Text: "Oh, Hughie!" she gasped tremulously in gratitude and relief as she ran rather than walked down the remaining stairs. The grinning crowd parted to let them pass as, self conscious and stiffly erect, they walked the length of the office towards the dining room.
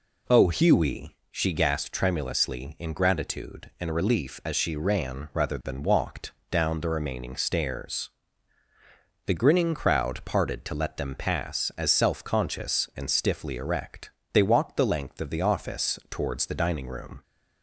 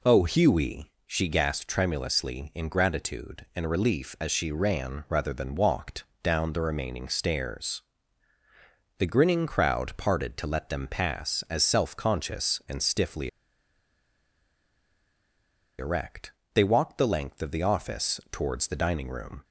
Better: first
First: pauses between "walked" and "down"; slight; at 6.3 s; 0.18 s long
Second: pauses between "walked" and "down"; slight; at 6.0 s; 0.18 s long // pauses between "stiffly" and "erect"; strong; at 13.2 s; 2.5 s long

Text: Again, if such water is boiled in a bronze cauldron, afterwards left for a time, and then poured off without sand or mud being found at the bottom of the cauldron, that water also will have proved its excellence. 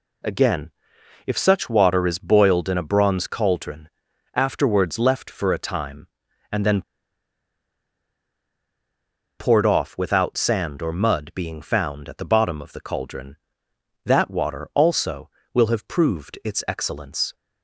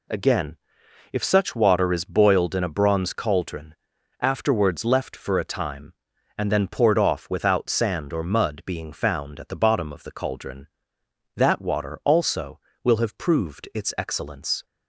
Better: second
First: pauses between "then" and "poured"; strong; at 6.8 s; 2.5 s long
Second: none

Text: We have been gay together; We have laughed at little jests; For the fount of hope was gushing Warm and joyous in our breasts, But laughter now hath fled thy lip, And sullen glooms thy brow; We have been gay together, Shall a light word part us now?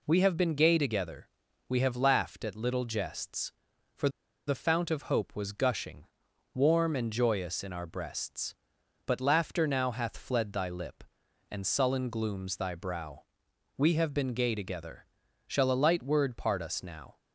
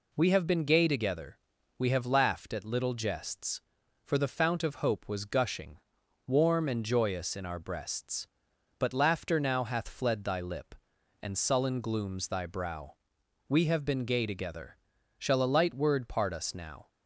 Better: second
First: pauses between "For" and "the"; at 4.0 s; 0.39 s long // pauses between "gushing" and "Warm"; noticeable; at 6.0 s; 0.50 s long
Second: pauses between "gushing" and "Warm"; noticeable; at 5.7 s; 0.50 s long

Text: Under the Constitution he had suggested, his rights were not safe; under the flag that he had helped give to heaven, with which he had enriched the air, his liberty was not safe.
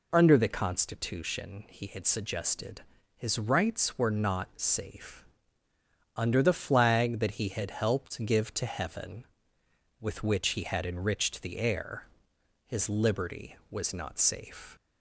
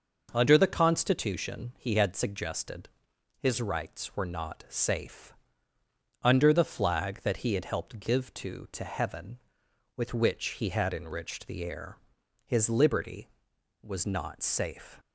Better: first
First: none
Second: starts louder than the rest; noticeable; until 1.3 s; 6 dB // says "to" twice; at 8.6 s

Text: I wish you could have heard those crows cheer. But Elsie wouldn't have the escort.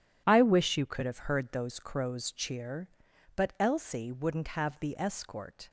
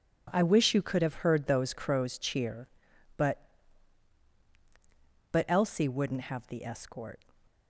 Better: first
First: none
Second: says "But" twice; at 5.3 s

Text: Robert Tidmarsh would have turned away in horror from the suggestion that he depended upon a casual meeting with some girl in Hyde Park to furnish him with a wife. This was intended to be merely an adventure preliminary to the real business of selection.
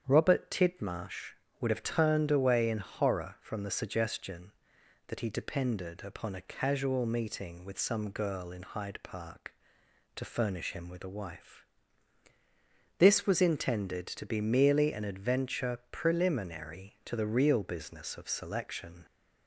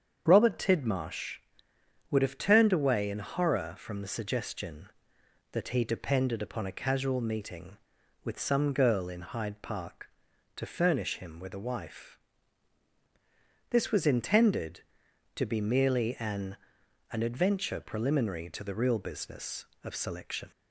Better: first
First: starts louder than the rest; strong; until 1.0 s; 8 dB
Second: starts louder than the rest; strong; until 1.2 s; 7.5 dB // says "an" twice; at 17.1 s

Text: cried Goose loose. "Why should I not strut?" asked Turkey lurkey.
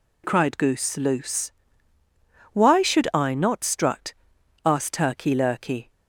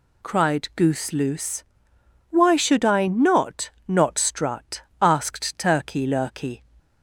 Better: first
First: none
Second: says "not" twice; at 3.8 s

